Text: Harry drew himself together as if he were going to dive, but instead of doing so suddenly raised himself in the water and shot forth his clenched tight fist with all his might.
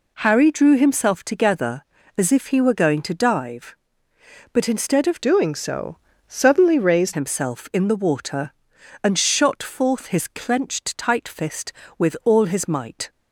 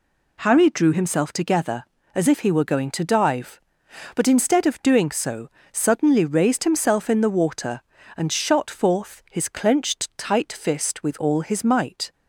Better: second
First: changes voice from "doing" to "raised"; from 5.2 to 7.1 s; 1.9 s long // pauses between "so" and "suddenly"; slight; at 5.9 s; 0.32 s long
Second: pauses between "so" and "suddenly"; slight; at 5.4 s; 0.24 s long

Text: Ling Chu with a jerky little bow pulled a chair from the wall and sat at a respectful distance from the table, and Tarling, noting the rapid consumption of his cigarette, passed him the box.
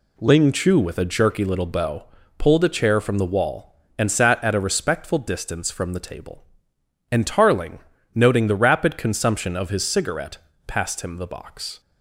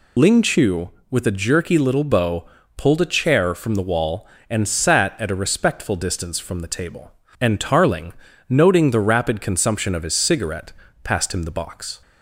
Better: first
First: pauses between "bow" and "pulled"; slight; at 2.0 s; 0.32 s long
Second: loses the start of "Ling"; at 0.1 s; 55 ms // pauses between "bow" and "pulled"; slight; at 2.4 s; 0.32 s long

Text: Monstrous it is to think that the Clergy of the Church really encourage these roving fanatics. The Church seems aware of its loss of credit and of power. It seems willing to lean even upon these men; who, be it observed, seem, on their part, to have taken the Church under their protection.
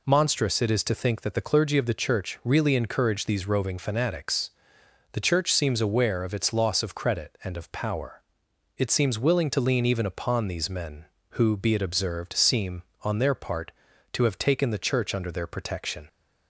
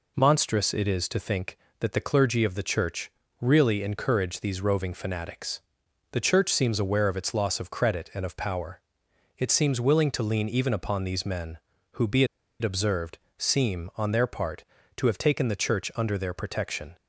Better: first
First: none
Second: pauses between "Church" and "really"; slight; at 3.1 s; 0.30 s long // pauses between "be" and "it"; slight; at 12.2 s; 0.35 s long

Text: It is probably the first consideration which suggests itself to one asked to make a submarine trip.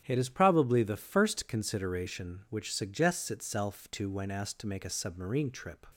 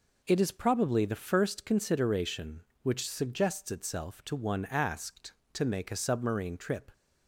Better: second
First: starts louder than the rest; strong; until 1.0 s; 10.5 dB // says "when" for "one"; at 4.1 s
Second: none

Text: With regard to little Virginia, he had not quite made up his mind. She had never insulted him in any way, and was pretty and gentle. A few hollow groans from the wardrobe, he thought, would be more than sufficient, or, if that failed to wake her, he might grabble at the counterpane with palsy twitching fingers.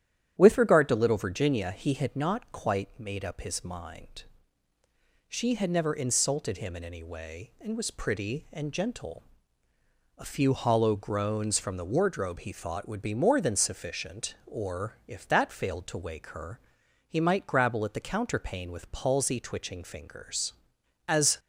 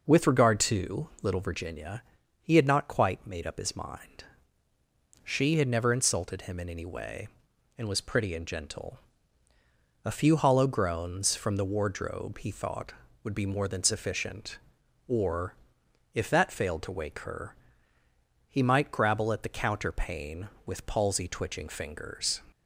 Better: second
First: starts louder than the rest; strong; until 1.4 s; 10.5 dB // goes on to say "As"; slight; from 21.0 s on; 0.30 s long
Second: none

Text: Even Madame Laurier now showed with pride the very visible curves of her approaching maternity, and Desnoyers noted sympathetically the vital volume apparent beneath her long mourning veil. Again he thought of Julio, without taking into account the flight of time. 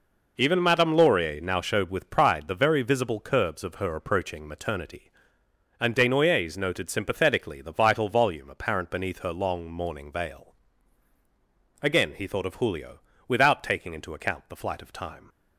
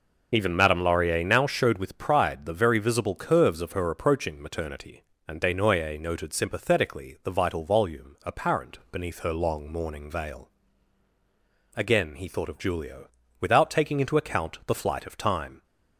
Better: first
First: none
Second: loses the start of "Even"; at 0.3 s; 25 ms

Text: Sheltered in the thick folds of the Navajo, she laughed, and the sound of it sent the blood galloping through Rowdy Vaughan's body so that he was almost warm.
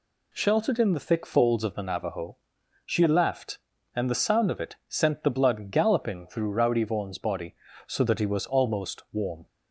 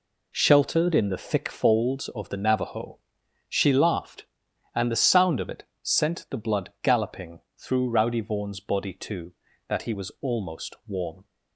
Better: first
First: none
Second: pauses between "it" and "sent"; slight; at 5.6 s; 0.18 s long // pauses between "galloping" and "through"; slight; at 7.4 s; 0.18 s long // says "too" for "so"; at 8.9 s

